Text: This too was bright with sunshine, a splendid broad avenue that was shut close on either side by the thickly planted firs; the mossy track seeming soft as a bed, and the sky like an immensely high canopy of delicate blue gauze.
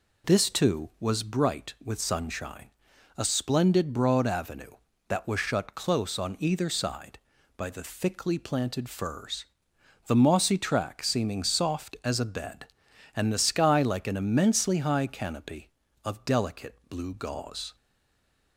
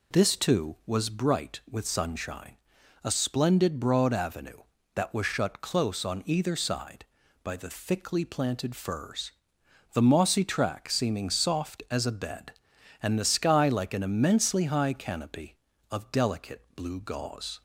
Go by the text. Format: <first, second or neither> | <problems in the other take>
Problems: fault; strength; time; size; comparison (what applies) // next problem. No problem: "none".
second | stays silent after the last word; slight; from 17.7 s on; 0.8 s long